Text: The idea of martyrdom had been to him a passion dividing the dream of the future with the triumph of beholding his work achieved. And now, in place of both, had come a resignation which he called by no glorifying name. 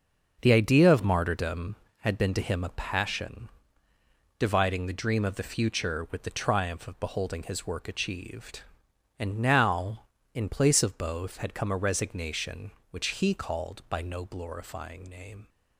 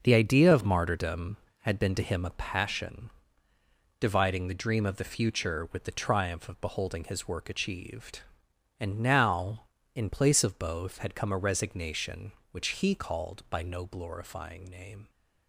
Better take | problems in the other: neither | pauses between "passion" and "dividing"; noticeable; the same in both

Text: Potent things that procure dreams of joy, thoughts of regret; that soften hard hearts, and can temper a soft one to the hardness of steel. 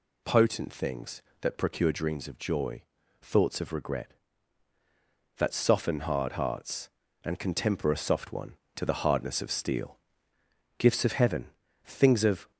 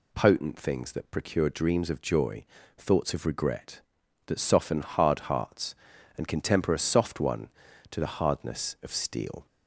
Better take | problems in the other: second | goes on to say "Gifts of heaven things of"; strong; from 10.7 s on; 1.7 s long

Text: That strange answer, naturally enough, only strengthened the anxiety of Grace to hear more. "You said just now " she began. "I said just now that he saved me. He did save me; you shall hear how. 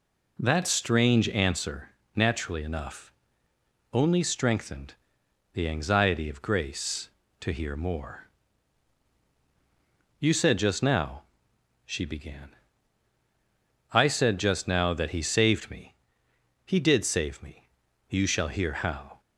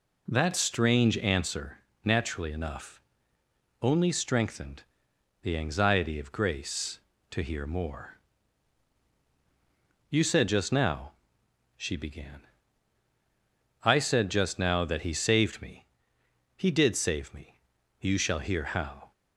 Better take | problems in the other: neither | pauses between "strengthened" and "the"; noticeable; the same in both

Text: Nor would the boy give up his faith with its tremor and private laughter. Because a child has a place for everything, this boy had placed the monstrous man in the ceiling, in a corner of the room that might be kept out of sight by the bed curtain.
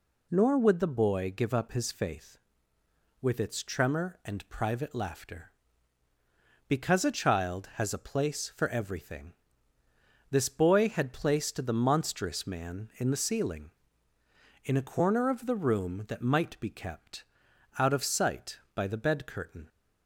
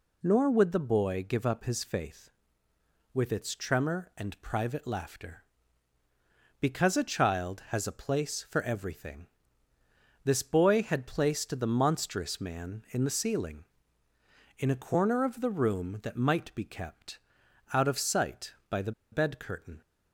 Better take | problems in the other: first | pauses between "kept" and "out"; noticeable; at 17.1 s; 0.54 s long; noticeable in the first // pauses between "the" and "bed"; slight; at 18.9 s; 0.21 s long

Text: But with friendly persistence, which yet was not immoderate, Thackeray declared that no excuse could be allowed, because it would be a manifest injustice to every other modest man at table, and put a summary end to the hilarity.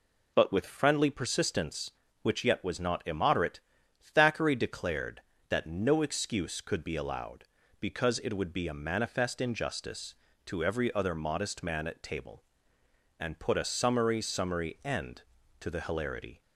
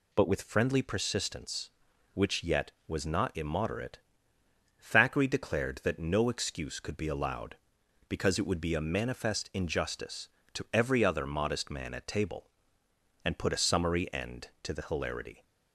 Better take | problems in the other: second | says "summary" twice; at 14.2 s

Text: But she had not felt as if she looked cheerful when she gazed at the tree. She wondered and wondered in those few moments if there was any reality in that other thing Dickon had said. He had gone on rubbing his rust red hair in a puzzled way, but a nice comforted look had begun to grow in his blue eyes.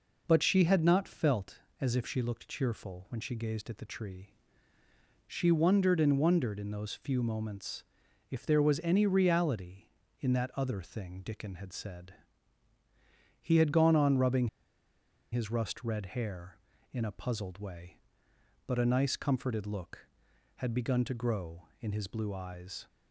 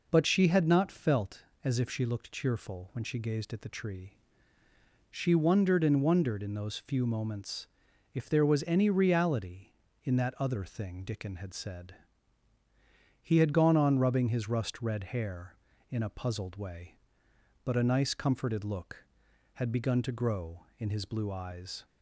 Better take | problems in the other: second | pauses between "moments" and "if"; noticeable; at 7.8 s; 0.48 s long; noticeable in the second // pauses between "rubbing" and "his"; noticeable; at 14.4 s; 0.85 s long

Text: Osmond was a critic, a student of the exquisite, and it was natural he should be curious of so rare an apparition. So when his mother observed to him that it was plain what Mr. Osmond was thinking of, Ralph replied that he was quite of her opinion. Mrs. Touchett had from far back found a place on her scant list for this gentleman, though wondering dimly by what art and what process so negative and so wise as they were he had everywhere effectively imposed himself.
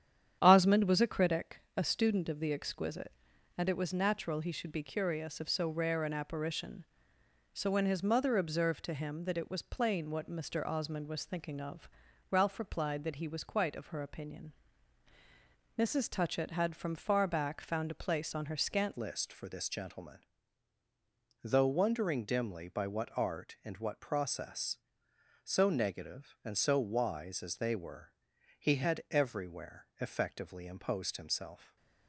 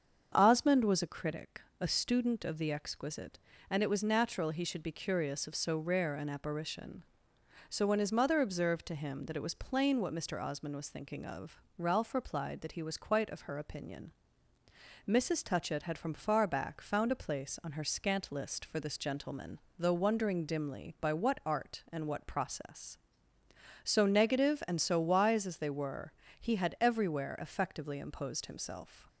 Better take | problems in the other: second | starts louder than the rest; strong; until 1.4 s; 9.5 dB; also in the second // changes voice at "list"; from 18.9 s on; 12.8 s long // pauses between "were" and "he"; at 28.1 s; 0.42 s long; slight in the second

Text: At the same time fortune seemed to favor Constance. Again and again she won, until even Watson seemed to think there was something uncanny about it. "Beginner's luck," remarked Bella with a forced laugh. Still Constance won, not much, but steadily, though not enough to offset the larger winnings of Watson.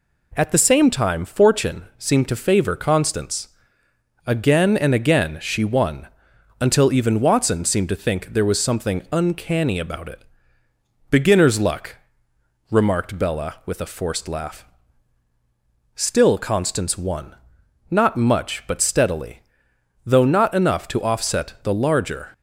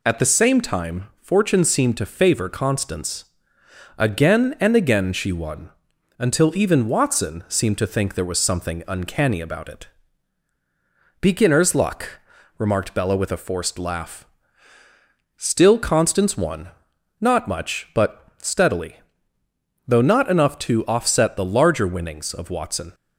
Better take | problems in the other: second | stops before "winnings of Watson"; at 22.3 s

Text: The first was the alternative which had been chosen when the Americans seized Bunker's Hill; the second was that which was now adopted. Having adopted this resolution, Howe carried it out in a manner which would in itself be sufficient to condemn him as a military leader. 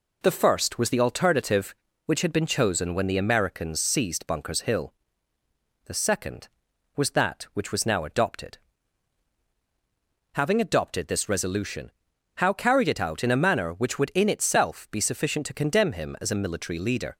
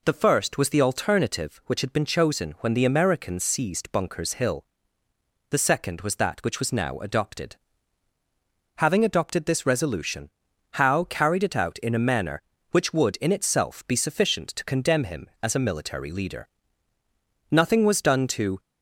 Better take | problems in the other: first | goes on to say "Nothing was done to"; noticeable; from 17.5 s on; 1.0 s long

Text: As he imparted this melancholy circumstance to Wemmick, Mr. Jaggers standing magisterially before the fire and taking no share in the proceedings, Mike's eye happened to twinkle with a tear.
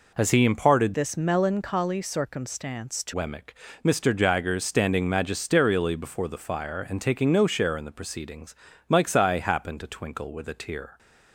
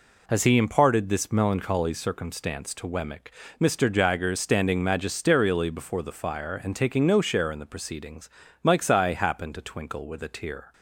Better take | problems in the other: second | changes voice from "this" to "to"; from 0.9 to 3.1 s; 2.2 s long

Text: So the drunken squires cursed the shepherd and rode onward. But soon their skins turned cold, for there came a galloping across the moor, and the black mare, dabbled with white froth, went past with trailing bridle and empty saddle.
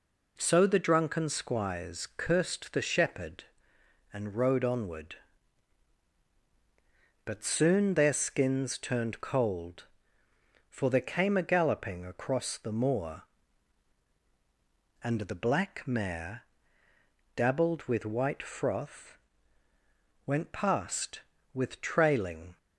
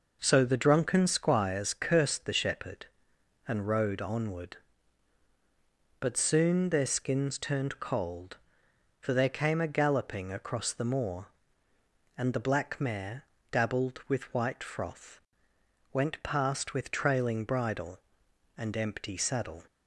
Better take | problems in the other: second | stops before "bridle and empty saddle"; at 22.5 s

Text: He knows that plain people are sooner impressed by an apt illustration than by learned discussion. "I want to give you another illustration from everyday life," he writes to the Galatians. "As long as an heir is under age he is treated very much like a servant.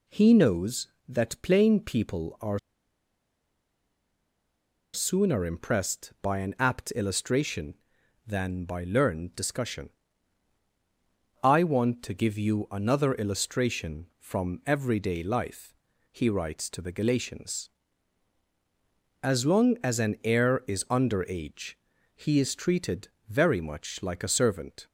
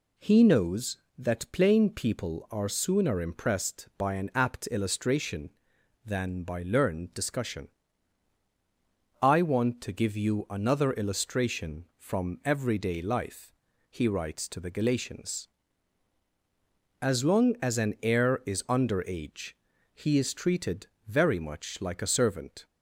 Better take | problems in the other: second | pauses between "are" and "sooner"; strong; at 2.5 s; 2.3 s long // pauses between "age" and "he"; at 21.7 s; 0.38 s long; also in the second // pauses between "treated" and "very"; slight; at 23.0 s; 0.20 s long; slight in the second

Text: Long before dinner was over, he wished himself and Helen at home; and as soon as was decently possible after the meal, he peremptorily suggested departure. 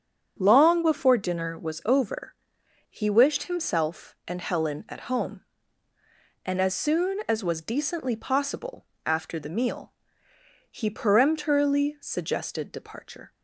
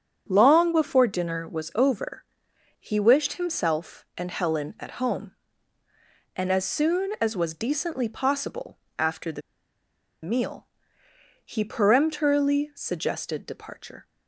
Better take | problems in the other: first | starts louder than the rest; until 1.3 s; 7 dB; also in the first // pauses between "possible" and "after"; slight; at 8.7 s; 0.22 s long; slight in the first // pauses between "the" and "meal"; noticeable; at 9.4 s; 0.81 s long

